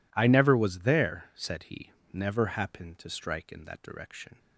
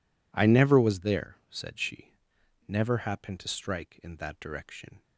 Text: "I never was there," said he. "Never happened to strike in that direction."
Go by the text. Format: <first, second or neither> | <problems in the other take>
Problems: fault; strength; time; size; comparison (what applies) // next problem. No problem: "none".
first | says "she" for "he"; at 1.7 s